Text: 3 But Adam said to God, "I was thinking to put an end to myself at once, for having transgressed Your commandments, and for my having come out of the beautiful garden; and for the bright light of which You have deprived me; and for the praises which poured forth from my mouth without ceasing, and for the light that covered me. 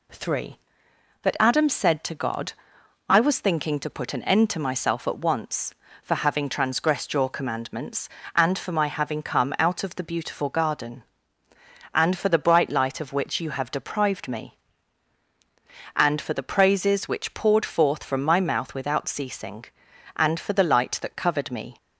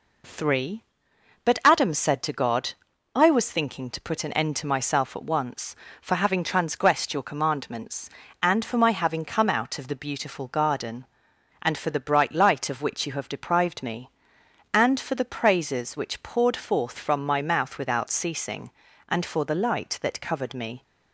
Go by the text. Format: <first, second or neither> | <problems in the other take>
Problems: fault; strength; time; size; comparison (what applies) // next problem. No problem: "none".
neither | none